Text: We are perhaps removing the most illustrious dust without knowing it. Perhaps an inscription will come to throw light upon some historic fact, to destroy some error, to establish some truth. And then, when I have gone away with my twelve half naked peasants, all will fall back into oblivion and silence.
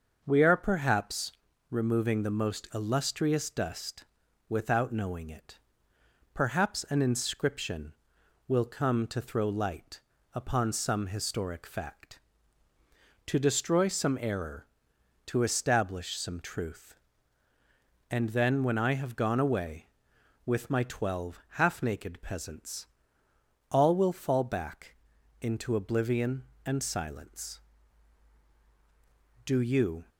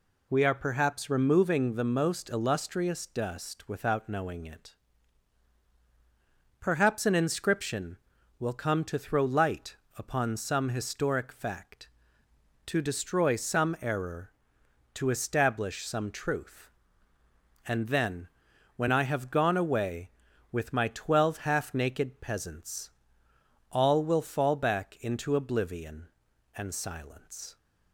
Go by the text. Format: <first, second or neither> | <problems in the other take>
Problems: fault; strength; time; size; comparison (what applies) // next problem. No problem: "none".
second | starts louder than the rest; until 1.2 s; 6.5 dB // pauses between "perhaps" and "removing"; slight; at 1.3 s; 0.36 s long // pauses between "dust" and "without"; at 4.0 s; 0.44 s long // pauses between "light" and "upon"; slight; at 9.9 s; 0.34 s long; slight in the second // pauses between "twelve" and "half"; slight; at 21.3 s; 0.18 s long // pauses between "back" and "into"; noticeable; at 24.9 s; 0.46 s long // goes on to say "Do you"; noticeable; from 29.4 s on; 0.62 s long